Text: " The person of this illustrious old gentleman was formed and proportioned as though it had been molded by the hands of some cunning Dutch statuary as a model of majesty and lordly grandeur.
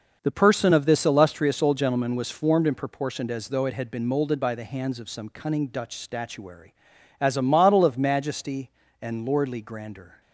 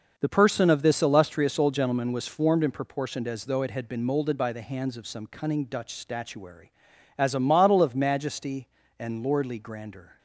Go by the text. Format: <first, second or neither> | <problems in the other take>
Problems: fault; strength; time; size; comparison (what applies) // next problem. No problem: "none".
neither | none